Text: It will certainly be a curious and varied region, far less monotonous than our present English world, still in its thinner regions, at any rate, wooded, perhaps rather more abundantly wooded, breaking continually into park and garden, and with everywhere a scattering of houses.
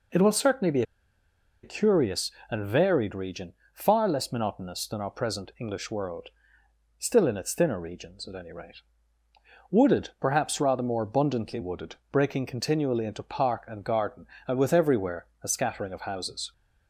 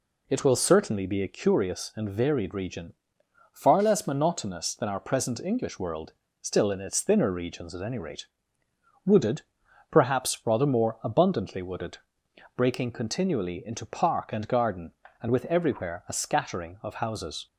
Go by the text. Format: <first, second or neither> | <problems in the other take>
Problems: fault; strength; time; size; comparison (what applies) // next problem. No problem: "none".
second | pauses between "be" and "a"; noticeable; at 0.8 s; 0.80 s long // pauses between "everywhere" and "a"; slight; at 15.2 s; 0.16 s long